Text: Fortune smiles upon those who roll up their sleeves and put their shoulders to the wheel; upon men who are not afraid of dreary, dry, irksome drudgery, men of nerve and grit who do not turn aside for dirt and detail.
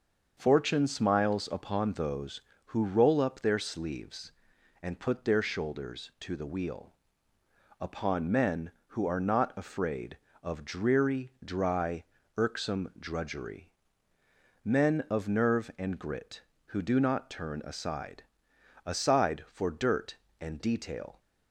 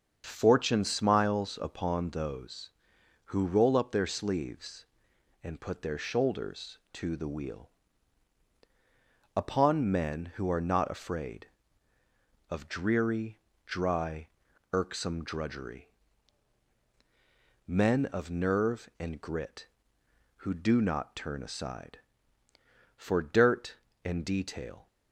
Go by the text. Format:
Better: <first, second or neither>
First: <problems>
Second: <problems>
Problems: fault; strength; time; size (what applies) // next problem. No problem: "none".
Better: second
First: starts louder than the rest; until 1.3 s; 6.5 dB // says "aside" twice; at 18.8 s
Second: starts louder than the rest; until 1.2 s; 7 dB